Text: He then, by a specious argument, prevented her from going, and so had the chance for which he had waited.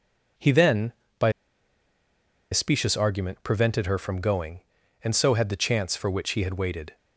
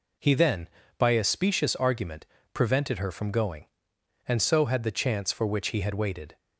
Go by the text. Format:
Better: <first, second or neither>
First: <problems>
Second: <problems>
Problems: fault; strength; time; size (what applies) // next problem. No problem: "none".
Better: second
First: pauses between "by" and "a"; at 1.3 s; 1.2 s long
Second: none